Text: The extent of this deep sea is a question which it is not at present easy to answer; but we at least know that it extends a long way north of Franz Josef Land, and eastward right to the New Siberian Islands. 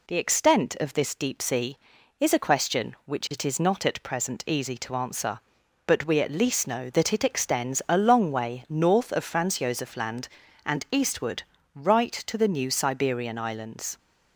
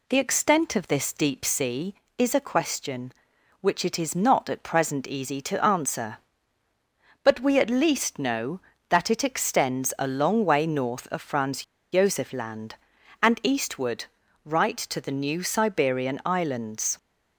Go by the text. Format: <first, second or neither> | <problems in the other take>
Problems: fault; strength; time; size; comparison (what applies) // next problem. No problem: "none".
first | pauses between "Franz" and "Josef"; slight; at 11.6 s; 0.28 s long // pauses between "eastward" and "right"; at 14.0 s; 0.38 s long; slight in the first